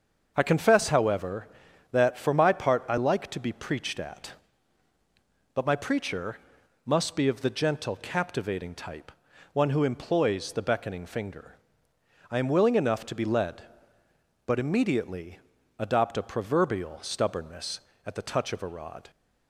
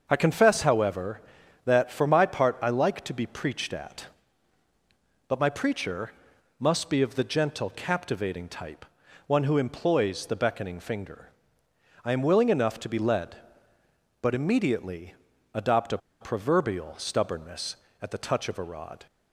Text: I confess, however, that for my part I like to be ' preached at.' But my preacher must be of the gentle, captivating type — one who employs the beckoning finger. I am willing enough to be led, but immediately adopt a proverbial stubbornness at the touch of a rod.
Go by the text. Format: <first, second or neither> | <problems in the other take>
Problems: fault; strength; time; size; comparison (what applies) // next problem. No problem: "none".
first | starts louder than the rest; until 1.1 s; 6.5 dB; also in the first // pauses between "preacher" and "must"; noticeable; at 6.1 s; 0.48 s long; noticeable in the first // pauses between "immediately" and "adopt"; at 15.1 s; 0.40 s long; also in the first // pauses between "a" and "proverbial"; slight; at 15.9 s; 0.23 s long